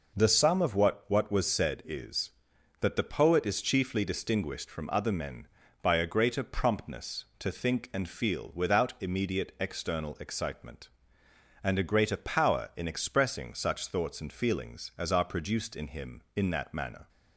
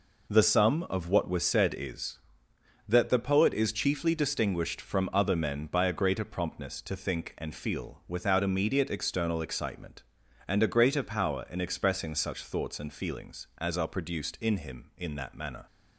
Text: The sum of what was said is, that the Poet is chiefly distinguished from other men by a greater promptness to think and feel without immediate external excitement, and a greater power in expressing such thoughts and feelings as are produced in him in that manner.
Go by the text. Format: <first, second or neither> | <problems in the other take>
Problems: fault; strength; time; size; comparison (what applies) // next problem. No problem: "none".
second | says "what" twice; at 1.0 s